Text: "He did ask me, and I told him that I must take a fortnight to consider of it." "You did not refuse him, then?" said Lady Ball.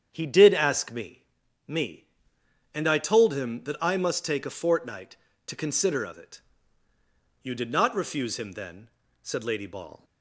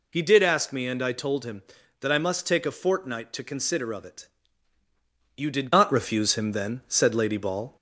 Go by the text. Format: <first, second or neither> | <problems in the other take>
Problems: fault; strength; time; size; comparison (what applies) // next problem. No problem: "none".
second | starts louder than the rest; strong; until 1.1 s; 8 dB // says "me" twice; at 1.6 s